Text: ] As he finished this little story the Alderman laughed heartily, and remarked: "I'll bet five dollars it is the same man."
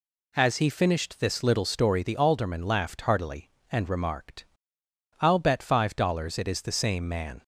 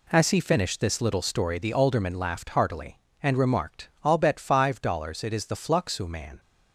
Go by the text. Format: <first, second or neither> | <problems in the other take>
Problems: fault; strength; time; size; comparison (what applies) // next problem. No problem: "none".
first | says "fluxu" for "same"; at 5.5 s